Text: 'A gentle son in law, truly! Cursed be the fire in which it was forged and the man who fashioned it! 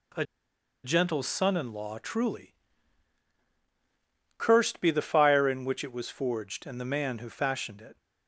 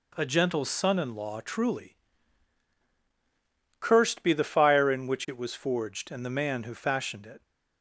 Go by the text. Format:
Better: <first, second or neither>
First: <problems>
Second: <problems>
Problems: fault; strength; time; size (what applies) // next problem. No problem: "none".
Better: second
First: pauses between "A" and "gentle"; noticeable; at 0.2 s; 0.59 s long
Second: none